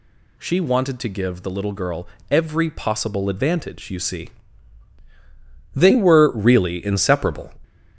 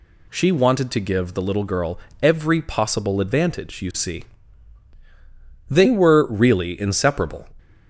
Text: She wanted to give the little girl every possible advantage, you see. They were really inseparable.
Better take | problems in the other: second | gets louder; noticeable; throughout; 5.5 dB // pauses between "girl" and "every"; slight; at 2.0 s; 0.22 s long; slight in the second

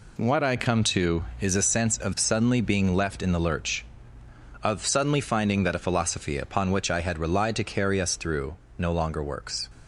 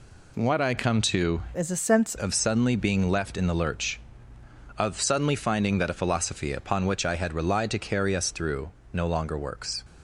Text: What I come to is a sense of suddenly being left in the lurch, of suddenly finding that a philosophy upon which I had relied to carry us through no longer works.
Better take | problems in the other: first | changes voice from "is" to "sense"; from 1.5 to 2.1 s; 0.6 s long // pauses between "through" and "no"; slight; at 8.7 s; 0.22 s long; slight in the first

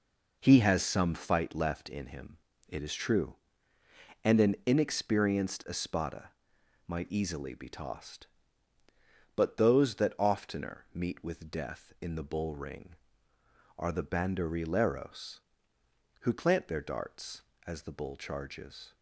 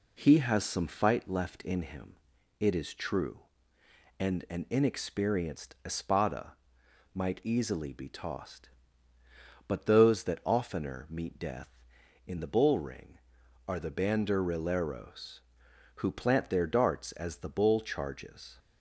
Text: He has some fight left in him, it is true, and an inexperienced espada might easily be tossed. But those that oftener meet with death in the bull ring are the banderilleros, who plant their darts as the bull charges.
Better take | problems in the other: first | pauses between "espada" and "might"; noticeable; at 6.5 s; 0.58 s long; noticeable in the first // skips "with"; at 11.3 s

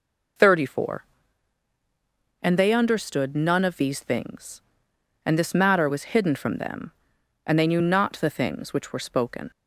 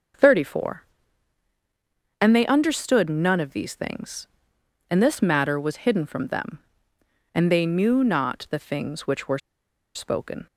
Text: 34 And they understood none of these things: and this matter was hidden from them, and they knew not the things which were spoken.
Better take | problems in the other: first | starts louder than the rest; until 2.5 s; 6 dB // pauses between "were" and "spoken"; noticeable; at 9.3 s; 0.57 s long

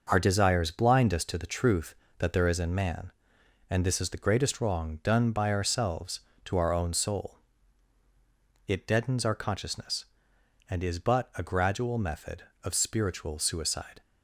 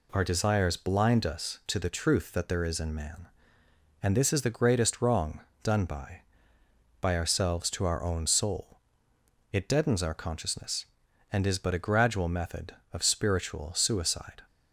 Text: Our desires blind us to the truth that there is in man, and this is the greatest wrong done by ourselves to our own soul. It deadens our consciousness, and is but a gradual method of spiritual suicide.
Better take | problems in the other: first | pauses between "wrong" and "done"; slight; at 5.4 s; 0.22 s long // says "by" twice; at 7.0 s

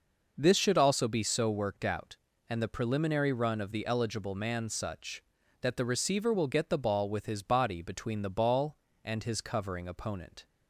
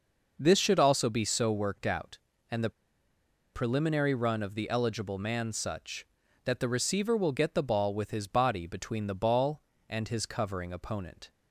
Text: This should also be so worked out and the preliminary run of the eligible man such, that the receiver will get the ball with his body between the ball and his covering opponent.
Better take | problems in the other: first | pauses between "the" and "preliminary"; noticeable; at 2.7 s; 0.83 s long

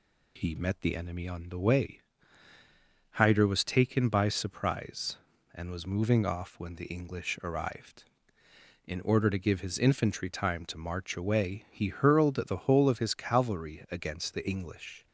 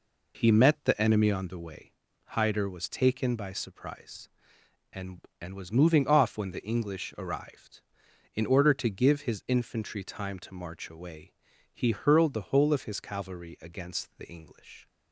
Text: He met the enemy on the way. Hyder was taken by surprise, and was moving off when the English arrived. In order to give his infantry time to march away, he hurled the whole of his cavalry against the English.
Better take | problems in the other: first | says "and" twice; at 5.3 s

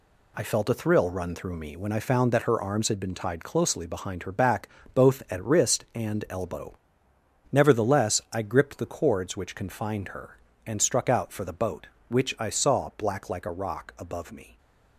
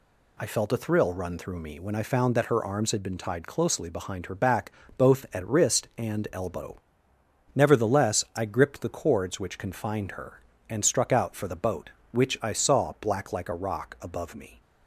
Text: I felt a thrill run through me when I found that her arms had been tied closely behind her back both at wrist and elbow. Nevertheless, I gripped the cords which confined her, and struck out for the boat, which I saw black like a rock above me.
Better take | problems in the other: second | gets quieter; throughout; 6.5 dB // pauses between "back" and "both"; slight; at 4.6 s; 0.26 s long; slight in the second

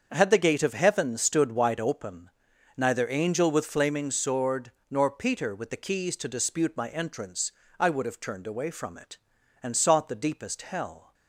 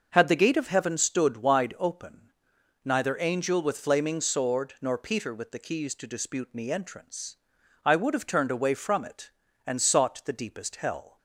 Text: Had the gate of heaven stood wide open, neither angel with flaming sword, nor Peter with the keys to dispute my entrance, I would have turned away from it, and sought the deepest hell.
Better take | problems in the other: first | starts louder than the rest; until 1.1 s; 6 dB; also in the first // says "me" for "my"; at 6.5 s

